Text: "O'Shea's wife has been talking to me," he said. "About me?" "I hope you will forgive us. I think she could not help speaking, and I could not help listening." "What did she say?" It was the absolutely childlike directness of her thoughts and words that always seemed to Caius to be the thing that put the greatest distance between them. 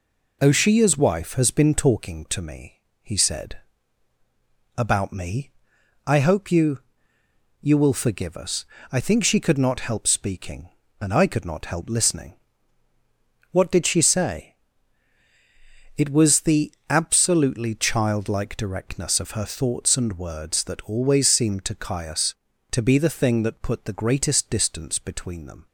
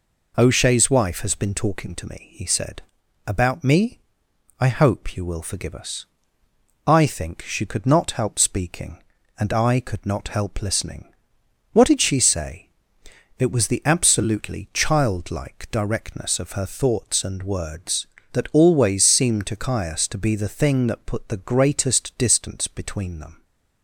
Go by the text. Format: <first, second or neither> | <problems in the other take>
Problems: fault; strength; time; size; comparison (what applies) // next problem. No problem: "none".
second | says "you" twice; at 7.6 s // pauses between "the" and "absolutely"; slight; at 16.7 s; 0.16 s long